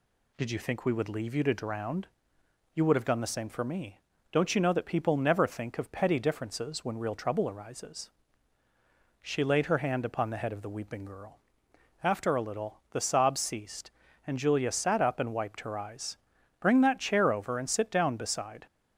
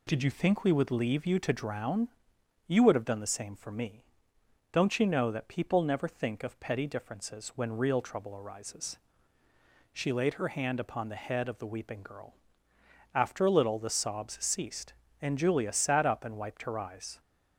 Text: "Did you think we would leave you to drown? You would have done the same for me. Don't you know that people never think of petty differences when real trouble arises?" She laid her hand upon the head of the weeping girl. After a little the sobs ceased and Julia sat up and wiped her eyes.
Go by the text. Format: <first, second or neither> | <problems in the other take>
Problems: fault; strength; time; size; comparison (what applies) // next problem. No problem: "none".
second | goes on to say "Bring that chair over and sit down beside"; strong; from 16.6 s on; 2.0 s long